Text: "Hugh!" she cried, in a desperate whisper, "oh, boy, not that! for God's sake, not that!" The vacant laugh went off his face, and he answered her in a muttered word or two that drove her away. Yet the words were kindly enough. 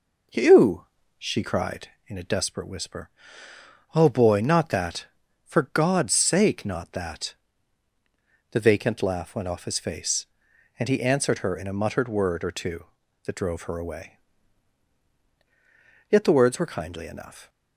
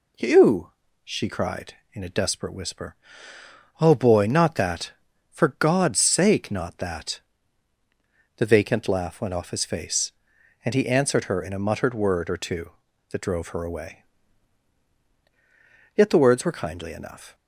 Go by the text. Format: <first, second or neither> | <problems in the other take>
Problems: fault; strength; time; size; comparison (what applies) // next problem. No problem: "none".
second | starts louder than the rest; noticeable; until 2.1 s; 5 dB